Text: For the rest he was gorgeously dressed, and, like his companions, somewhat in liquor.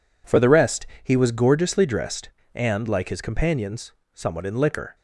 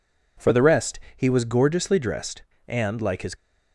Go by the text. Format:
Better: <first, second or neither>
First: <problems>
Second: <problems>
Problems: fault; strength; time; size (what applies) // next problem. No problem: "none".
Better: first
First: pauses between "rest" and "he"; slight; at 0.8 s; 0.16 s long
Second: pauses between "rest" and "he"; slight; at 1.0 s; 0.16 s long // stops before "companions somewhat in liquor"; at 3.3 s